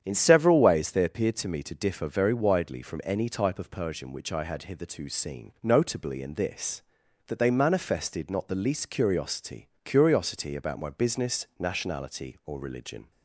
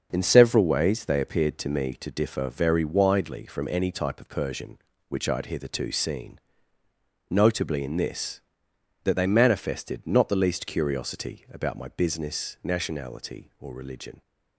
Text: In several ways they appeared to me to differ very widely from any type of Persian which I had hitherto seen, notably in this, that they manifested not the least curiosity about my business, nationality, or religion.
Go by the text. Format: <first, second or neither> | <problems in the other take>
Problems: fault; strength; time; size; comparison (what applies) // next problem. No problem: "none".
second | starts louder than the rest; strong; until 1.0 s; 9 dB; also in the second // says "curiosity" twice; at 9.8 s